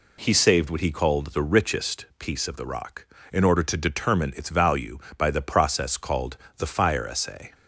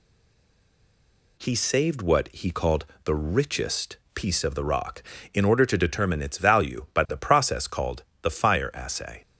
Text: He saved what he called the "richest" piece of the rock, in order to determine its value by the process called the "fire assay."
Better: first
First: pauses between "called" and "the"; slight; at 6.3 s; 0.20 s long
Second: stays silent before the first word; noticeable; until 1.3 s; 1.3 s long // pauses between "called" and "the"; slight; at 2.8 s; 0.20 s long // pauses between "richest" and "piece"; slight; at 3.9 s; 0.18 s long // pauses between "called" and "the"; slight; at 8.0 s; 0.18 s long

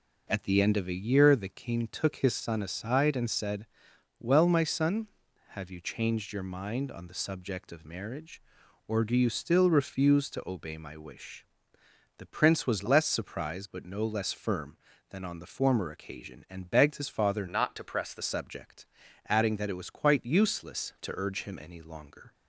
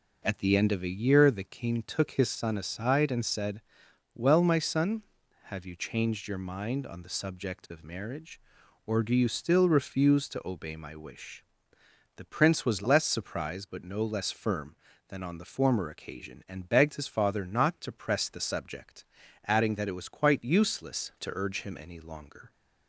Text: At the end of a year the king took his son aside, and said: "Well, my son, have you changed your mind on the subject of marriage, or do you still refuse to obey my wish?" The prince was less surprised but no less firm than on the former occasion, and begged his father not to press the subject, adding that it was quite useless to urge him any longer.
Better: second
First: changes voice from "not" to "the"; from 17.4 to 18.2 s; 0.8 s long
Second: none

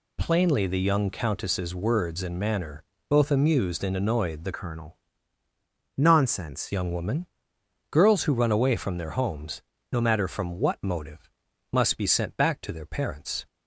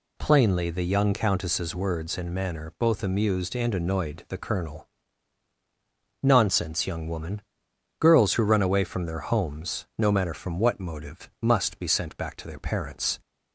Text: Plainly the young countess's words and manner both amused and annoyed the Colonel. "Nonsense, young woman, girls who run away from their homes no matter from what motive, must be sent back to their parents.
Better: second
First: pauses between "manner" and "both"; slight; at 2.8 s; 0.26 s long // changes voice from "Colonel" to "Nonsense"; from 4.5 to 6.7 s; 2.2 s long // pauses between "homes" and "no"; slight; at 9.6 s; 0.30 s long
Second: none

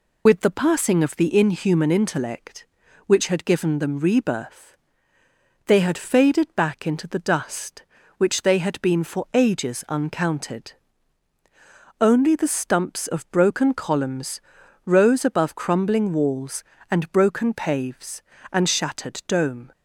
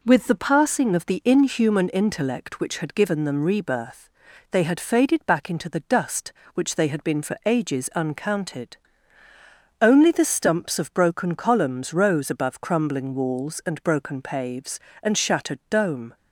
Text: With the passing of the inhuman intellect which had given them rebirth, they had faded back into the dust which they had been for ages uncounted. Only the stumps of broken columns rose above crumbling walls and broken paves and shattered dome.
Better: second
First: loses the start of "With"; at 0.2 s; 40 ms // pauses between "columns" and "rose"; at 14.4 s; 0.42 s long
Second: none

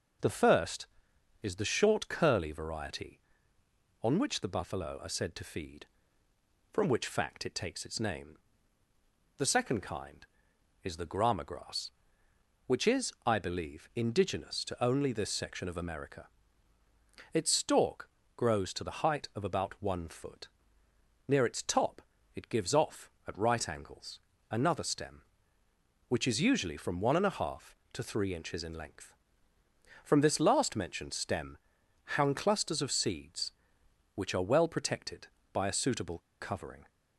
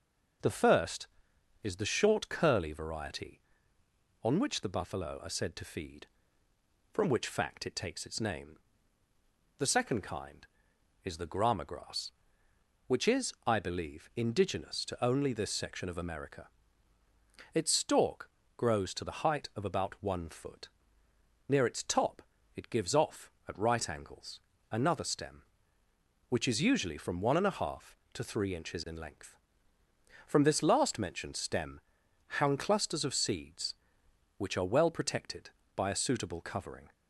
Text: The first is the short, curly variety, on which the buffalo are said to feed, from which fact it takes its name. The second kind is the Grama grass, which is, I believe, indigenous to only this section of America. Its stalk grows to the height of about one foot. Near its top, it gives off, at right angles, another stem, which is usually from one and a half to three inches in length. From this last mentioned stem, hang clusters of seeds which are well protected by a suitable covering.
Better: second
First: pauses between "stalk" and "grows"; slight; at 18.0 s; 0.30 s long // pauses between "suitable" and "covering"; slight; at 36.1 s; 0.21 s long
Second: pauses between "stalk" and "grows"; slight; at 18.2 s; 0.30 s long

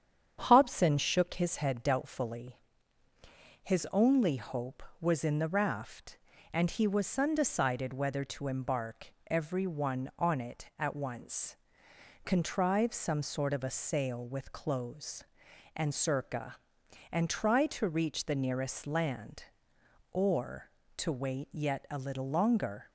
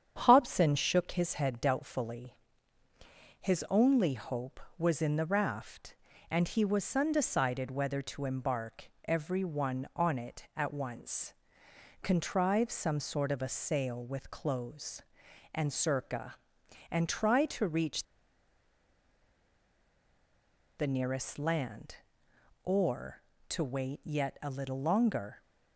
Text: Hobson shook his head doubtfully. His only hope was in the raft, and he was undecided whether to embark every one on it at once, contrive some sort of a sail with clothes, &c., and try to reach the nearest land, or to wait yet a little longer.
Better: first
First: starts louder than the rest; strong; until 1.4 s; 8 dB // pauses between "embark" and "every"; slight; at 9.1 s; 0.16 s long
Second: starts louder than the rest; strong; until 1.2 s; 8 dB // pauses between "embark" and "every"; slight; at 8.8 s; 0.16 s long // pauses between "reach" and "the"; strong; at 18.0 s; 2.7 s long

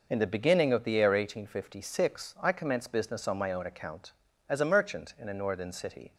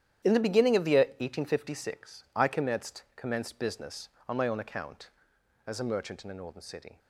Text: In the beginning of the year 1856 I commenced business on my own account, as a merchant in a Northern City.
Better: first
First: none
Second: starts louder than the rest; strong; until 1.3 s; 10.5 dB // says "commenced" twice; at 3.1 s

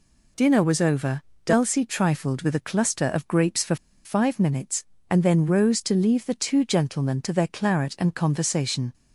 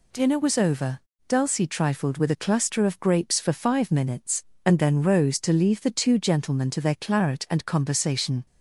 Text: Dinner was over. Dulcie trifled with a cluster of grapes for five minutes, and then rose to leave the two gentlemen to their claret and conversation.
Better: second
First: pauses between "for" and "five"; slight; at 3.7 s; 0.28 s long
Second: none

